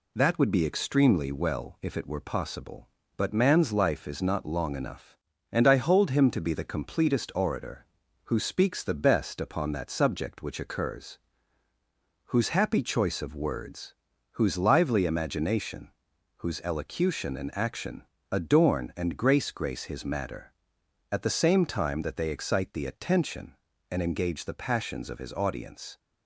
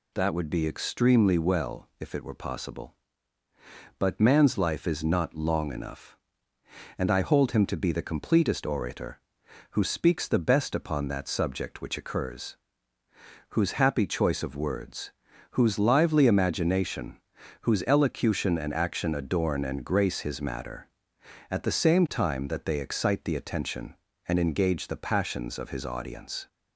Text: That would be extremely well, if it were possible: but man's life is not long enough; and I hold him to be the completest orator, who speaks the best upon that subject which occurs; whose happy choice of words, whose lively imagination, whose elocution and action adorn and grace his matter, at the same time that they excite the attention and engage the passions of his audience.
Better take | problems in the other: second | pauses between "action" and "adorn"; slight; at 18.0 s; 0.26 s long // says "grace" twice; at 19.5 s

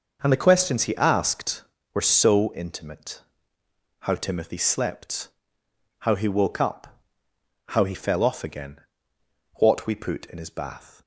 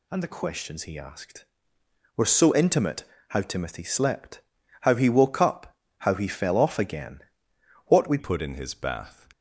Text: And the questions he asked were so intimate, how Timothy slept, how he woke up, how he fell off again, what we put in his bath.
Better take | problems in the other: first | changes voice at "put"; from 8.1 s on; 1.1 s long

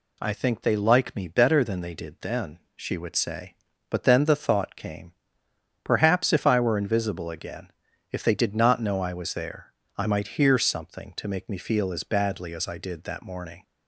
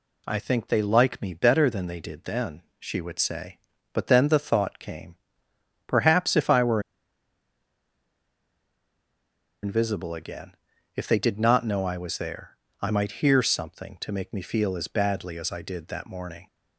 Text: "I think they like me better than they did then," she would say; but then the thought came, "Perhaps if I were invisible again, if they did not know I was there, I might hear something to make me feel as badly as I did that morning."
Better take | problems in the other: first | pauses between "were" and "invisible"; strong; at 6.7 s; 2.8 s long

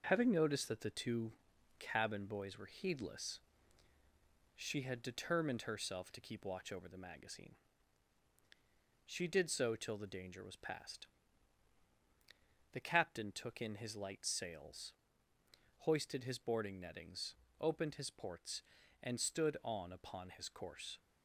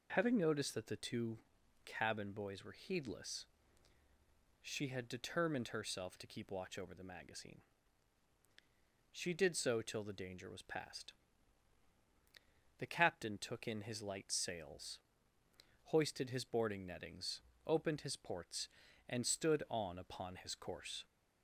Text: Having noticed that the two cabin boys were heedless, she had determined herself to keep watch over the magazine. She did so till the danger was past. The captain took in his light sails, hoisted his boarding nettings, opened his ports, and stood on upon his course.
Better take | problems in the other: second | gets quieter; noticeable; throughout; 4.5 dB // pauses between "two" and "cabin"; noticeable; at 1.3 s; 0.48 s long; noticeable in the second

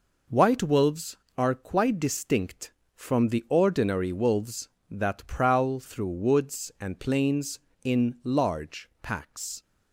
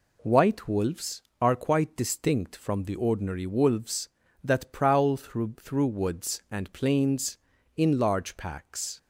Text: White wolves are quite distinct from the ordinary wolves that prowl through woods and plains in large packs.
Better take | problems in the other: first | says "through" twice; at 5.6 s

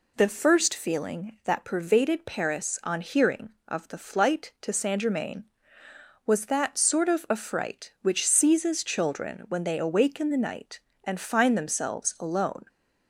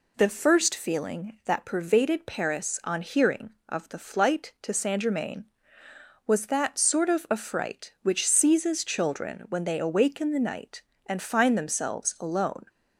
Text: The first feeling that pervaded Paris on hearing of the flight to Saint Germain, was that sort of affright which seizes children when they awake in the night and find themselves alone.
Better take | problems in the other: neither | none

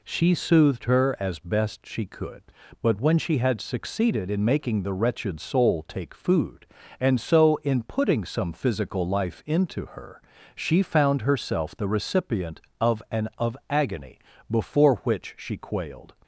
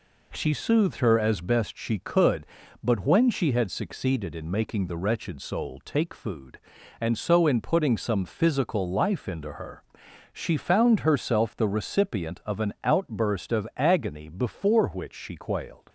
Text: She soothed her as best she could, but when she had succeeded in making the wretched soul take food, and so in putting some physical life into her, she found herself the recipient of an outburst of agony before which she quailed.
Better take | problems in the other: second | skips "outburst"; at 13.3 s // pauses between "agony" and "before"; slight; at 14.1 s; 0.32 s long

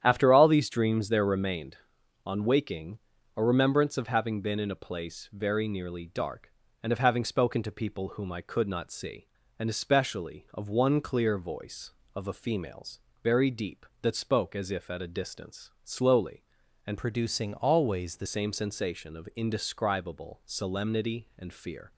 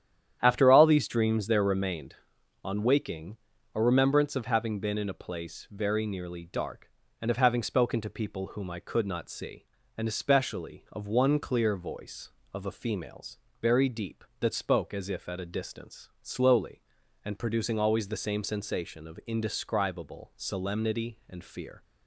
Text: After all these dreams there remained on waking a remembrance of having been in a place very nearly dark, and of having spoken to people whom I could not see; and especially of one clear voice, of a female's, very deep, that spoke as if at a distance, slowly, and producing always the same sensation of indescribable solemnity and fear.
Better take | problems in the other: second | starts louder than the rest; strong; until 1.0 s; 10 dB; strong in the second // pauses between "waking" and "a"; at 2.9 s; 0.38 s long; also in the second // changes voice from "producing" to "the"; from 16.9 to 18.2 s; 1.3 s long

